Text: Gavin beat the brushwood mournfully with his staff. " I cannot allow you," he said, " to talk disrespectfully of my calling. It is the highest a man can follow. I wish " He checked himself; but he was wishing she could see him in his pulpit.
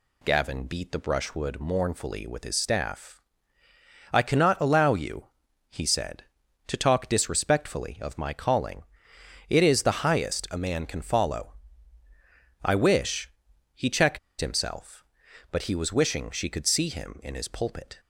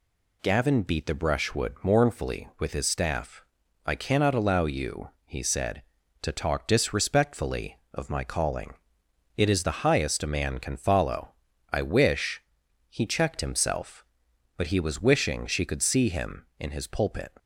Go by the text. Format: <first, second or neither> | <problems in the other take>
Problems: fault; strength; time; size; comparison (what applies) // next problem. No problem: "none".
second | pauses between "checked" and "himself"; slight; at 14.1 s; 0.21 s long